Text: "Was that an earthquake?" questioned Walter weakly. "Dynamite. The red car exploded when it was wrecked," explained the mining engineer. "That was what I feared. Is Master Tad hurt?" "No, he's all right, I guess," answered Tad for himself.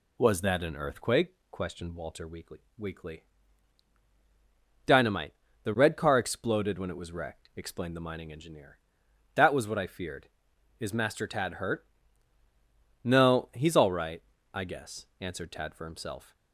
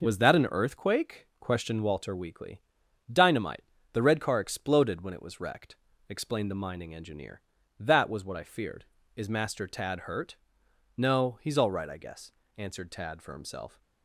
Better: second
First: says "weakly" twice; at 2.7 s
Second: none

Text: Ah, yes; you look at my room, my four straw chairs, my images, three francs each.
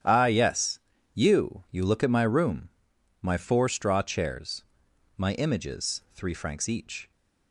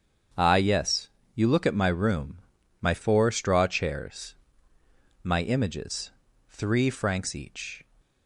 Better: second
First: starts louder than the rest; strong; until 1.3 s; 9.5 dB // says "you" twice; at 1.6 s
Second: starts louder than the rest; strong; until 1.6 s; 7.5 dB

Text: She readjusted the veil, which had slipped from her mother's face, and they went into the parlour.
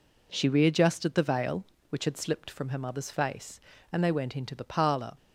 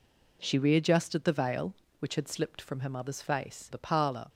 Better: first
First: none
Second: skips "and they went into"; at 3.7 s

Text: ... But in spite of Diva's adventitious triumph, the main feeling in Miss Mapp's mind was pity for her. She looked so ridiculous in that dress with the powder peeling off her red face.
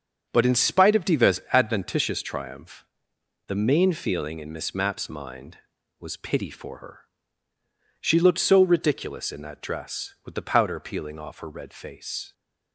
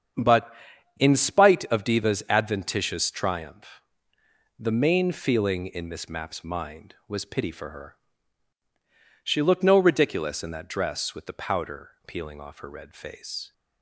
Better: first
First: starts louder than the rest; noticeable; until 1.3 s; 6 dB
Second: starts louder than the rest; strong; until 1.6 s; 7.5 dB // says "no" for "so"; at 9.6 s // pauses between "powder" and "peeling"; slight; at 11.9 s; 0.16 s long

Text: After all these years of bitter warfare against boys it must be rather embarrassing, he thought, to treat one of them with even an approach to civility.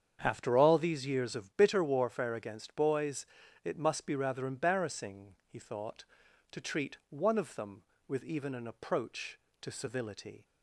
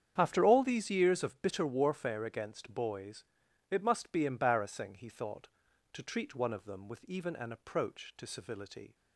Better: first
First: starts louder than the rest; strong; until 1.2 s; 7.5 dB // pauses between "boys" and "it"; at 3.2 s; 0.40 s long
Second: starts louder than the rest; strong; until 1.1 s; 8.5 dB // pauses between "boys" and "it"; noticeable; at 3.2 s; 0.46 s long // skips "rather"; at 4.2 s

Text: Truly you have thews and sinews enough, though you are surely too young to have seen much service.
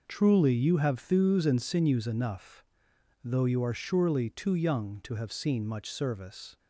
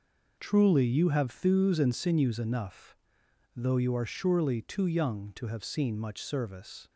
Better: neither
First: none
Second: none

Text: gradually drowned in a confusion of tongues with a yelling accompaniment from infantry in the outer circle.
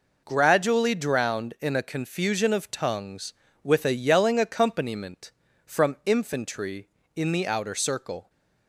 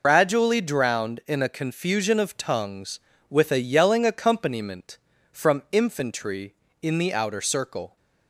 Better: first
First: none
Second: loses the start of "gradually"; at 0.0 s; 130 ms

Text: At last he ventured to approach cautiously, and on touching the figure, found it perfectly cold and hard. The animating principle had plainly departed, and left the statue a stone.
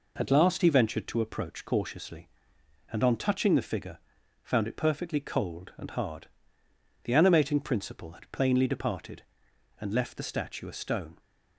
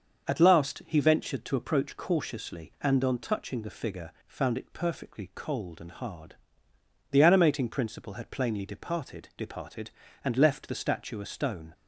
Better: first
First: none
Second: starts louder than the rest; until 1.3 s; 6.5 dB // says "departed" twice; at 9.3 s

